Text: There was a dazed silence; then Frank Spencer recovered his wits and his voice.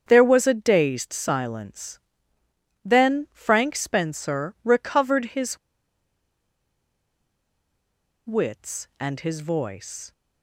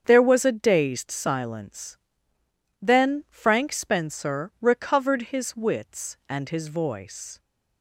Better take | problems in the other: second | starts louder than the rest; strong; until 1.0 s; 8 dB; strong in the second // pauses between "his" and "wits"; strong; at 5.5 s; 2.6 s long

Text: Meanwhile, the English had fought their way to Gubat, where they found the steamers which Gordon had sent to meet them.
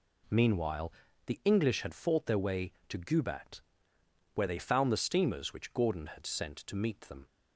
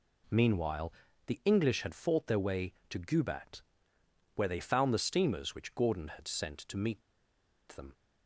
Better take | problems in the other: first | pauses between "meet" and "them"; noticeable; at 7.0 s; 0.67 s long

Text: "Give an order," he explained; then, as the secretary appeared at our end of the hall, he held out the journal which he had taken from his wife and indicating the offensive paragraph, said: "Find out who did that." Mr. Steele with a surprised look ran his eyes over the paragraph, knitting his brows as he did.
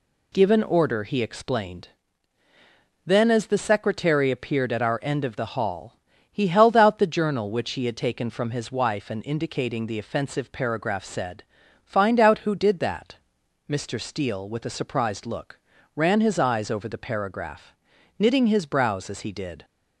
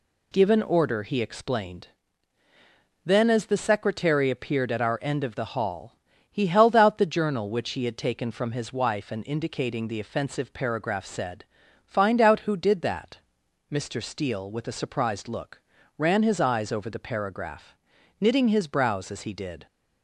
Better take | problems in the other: neither | pauses between "look" and "ran"; the same in both

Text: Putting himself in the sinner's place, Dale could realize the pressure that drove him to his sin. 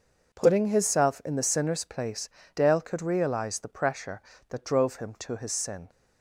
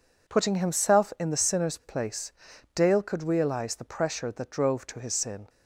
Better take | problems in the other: first | skips "him"; at 4.8 s

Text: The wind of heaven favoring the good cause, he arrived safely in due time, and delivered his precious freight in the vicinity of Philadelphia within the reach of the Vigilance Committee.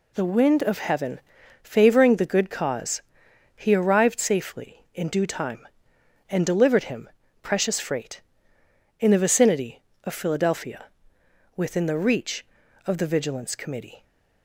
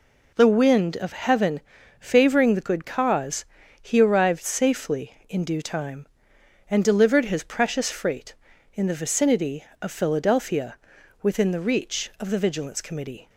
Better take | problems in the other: second | pauses between "heaven" and "favoring"; at 1.2 s; 0.42 s long; also in the second // says "him" for "his"; at 6.8 s // pauses between "Philadelphia" and "within"; noticeable; at 10.8 s; 0.68 s long; also in the second

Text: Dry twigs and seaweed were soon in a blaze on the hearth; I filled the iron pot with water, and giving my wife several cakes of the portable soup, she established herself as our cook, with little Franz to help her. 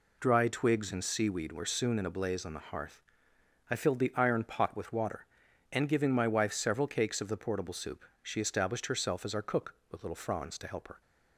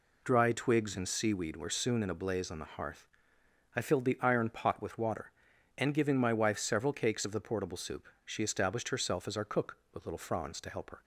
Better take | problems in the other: neither | none

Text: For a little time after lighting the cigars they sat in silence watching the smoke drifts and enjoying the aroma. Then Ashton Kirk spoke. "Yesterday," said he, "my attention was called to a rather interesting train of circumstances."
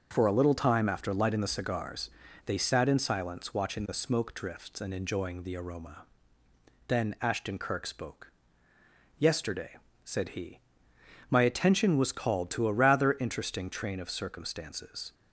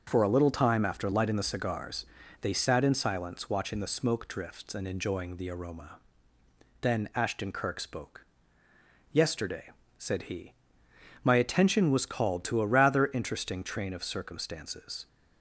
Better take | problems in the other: neither | starts louder than the rest; the same in both // pauses between "cigars" and "they"; slight; the same in both

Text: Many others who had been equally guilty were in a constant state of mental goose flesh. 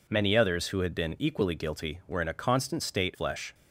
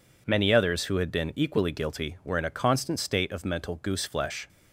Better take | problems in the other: second | skips "of mental goose"; at 3.1 s

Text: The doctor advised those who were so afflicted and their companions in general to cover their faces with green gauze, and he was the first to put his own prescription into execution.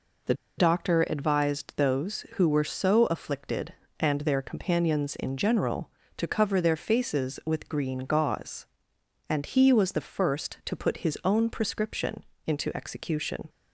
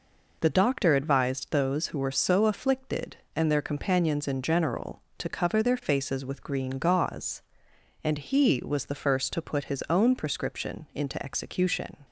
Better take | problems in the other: second | pauses between "The" and "doctor"; slight; at 0.3 s; 0.24 s long // pauses between "prescription" and "into"; slight; at 12.2 s; 0.22 s long

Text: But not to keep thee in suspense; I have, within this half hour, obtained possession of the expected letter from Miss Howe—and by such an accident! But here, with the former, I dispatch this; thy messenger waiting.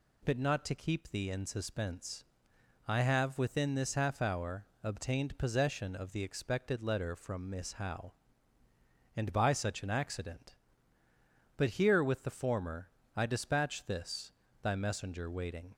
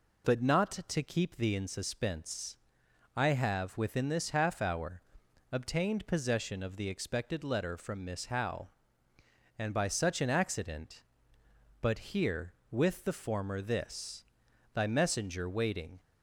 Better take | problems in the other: first | skips "I dispatch"; at 13.6 s

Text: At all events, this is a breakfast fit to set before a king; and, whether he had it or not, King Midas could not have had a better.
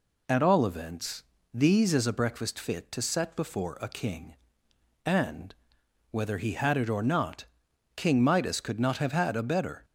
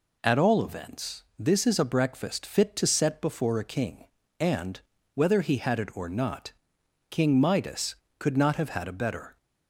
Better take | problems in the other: second | says "these" for "this"; at 1.5 s

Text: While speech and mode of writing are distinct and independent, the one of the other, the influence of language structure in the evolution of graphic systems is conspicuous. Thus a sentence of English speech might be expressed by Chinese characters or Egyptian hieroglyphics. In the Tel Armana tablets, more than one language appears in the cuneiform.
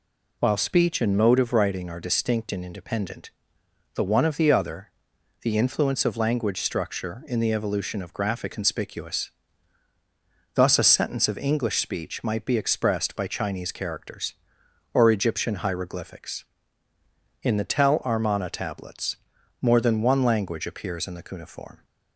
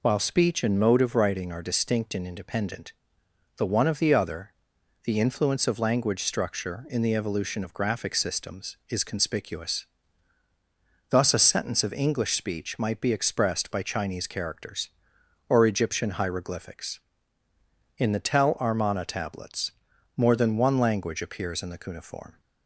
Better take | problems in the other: second | skips "systems is"; at 8.5 s

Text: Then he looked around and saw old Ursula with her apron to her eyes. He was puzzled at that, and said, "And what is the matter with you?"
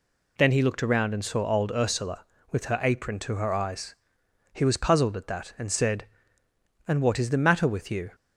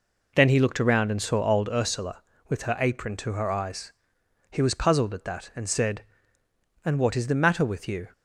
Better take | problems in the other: first | starts louder than the rest; noticeable; until 1.7 s; 4 dB

